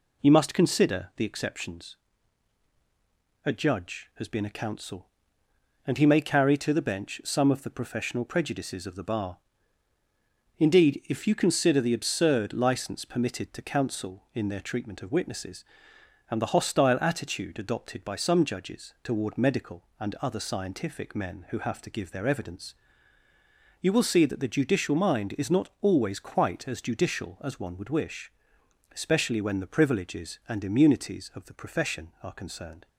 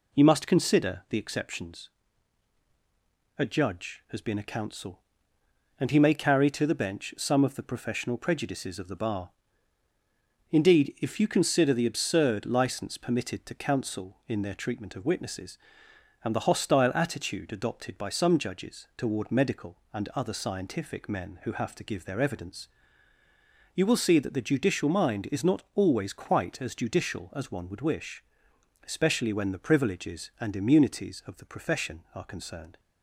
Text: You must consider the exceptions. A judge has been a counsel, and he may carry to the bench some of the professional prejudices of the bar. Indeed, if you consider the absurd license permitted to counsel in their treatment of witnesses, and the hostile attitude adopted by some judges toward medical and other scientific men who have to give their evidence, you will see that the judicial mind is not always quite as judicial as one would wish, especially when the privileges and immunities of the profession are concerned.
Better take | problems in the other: neither | none

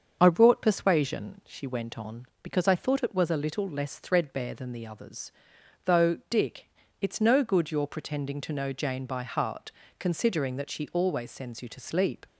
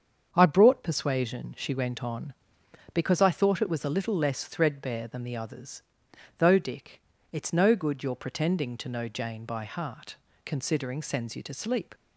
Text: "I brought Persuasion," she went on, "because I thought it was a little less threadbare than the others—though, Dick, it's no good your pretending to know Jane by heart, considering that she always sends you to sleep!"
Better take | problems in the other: first | starts louder than the rest; strong; until 1.3 s; 7 dB; also in the first // skips "that she always"; at 11.0 s

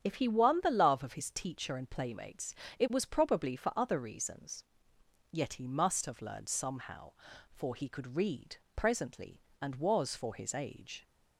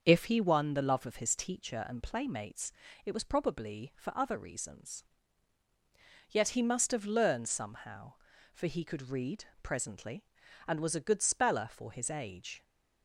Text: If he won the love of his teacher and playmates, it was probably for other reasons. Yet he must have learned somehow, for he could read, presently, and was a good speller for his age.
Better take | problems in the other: second | starts louder than the rest; strong; until 1.0 s; 8.5 dB; also in the second // skips "a good speller"; at 10.1 s

